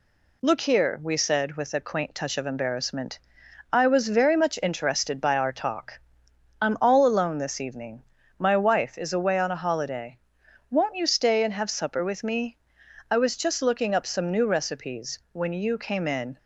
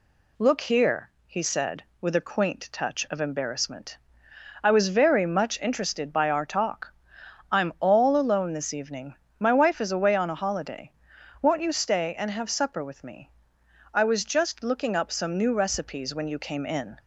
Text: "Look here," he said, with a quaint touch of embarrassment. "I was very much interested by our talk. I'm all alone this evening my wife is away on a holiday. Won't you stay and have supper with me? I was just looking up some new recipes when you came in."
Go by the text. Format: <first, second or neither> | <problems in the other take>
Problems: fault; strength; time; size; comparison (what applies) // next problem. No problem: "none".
second | says "we" for "he"; at 1.0 s // pauses between "evening" and "my"; slight; at 8.0 s; 0.34 s long; slight in the second // pauses between "recipes" and "when"; slight; at 15.1 s; 0.16 s long